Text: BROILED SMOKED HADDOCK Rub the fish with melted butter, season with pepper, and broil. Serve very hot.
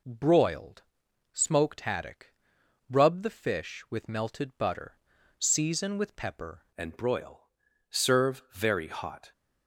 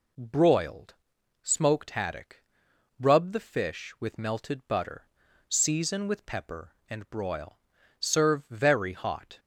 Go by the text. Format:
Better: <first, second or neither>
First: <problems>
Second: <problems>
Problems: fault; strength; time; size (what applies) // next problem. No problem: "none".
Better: second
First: pauses between "BROILED" and "SMOKED"; noticeable; at 0.8 s; 0.50 s long // pauses between "HADDOCK" and "Rub"; noticeable; at 2.3 s; 0.56 s long // changes voice at "and"; from 6.7 s on; 2.6 s long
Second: pauses between "BROILED" and "SMOKED"; noticeable; at 0.9 s; 0.48 s long // pauses between "HADDOCK" and "Rub"; noticeable; at 2.4 s; 0.56 s long